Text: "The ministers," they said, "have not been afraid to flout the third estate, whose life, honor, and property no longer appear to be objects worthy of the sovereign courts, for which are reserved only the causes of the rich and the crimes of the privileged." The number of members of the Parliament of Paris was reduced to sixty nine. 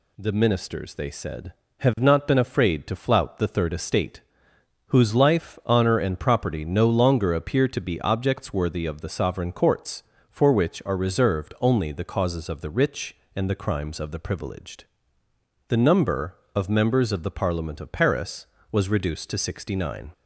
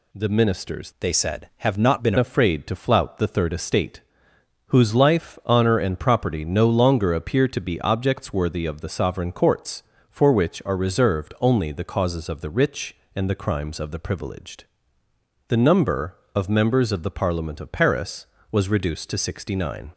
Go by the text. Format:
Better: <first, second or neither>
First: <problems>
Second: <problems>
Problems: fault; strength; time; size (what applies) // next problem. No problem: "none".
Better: first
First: none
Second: changes voice from "they" to "been"; from 1.0 to 2.1 s; 1.1 s long